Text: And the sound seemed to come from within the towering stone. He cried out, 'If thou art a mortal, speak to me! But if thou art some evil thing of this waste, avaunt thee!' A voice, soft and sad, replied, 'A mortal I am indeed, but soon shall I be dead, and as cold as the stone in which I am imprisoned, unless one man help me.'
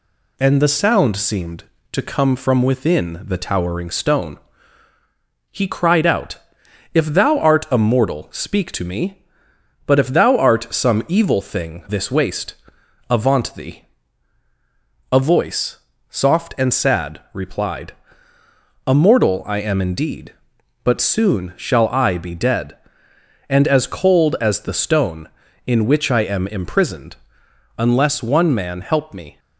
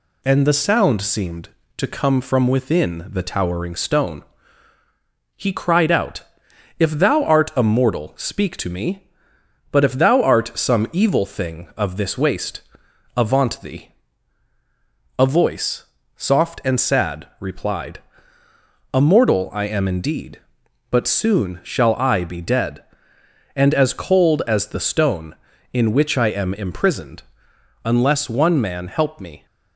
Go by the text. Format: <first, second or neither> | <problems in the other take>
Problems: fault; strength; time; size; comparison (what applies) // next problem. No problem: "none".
second | skips "of"; at 11.8 s